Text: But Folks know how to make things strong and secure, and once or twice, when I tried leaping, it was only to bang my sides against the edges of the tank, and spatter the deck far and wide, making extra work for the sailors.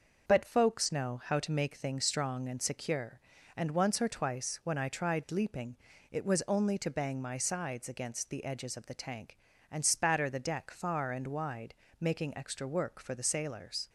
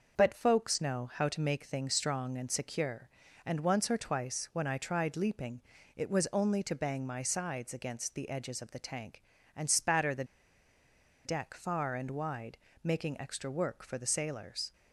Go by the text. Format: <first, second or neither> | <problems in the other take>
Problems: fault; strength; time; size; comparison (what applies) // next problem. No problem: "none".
first | starts louder than the rest; noticeable; until 1.2 s; 6 dB; noticeable in the first // pauses between "the" and "deck"; at 10.2 s; 1.0 s long